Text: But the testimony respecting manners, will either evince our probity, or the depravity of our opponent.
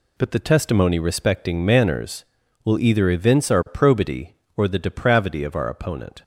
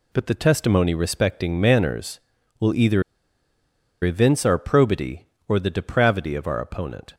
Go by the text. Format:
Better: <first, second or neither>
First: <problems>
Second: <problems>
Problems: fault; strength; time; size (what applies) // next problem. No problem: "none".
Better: first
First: none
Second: pauses between "either" and "evince"; at 3.0 s; 1.0 s long